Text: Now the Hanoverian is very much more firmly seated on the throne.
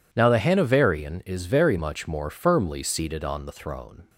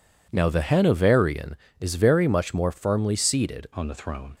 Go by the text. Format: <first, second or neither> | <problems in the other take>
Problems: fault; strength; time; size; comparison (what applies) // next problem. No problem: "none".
first | changes voice at "on"; from 3.7 s on; 0.6 s long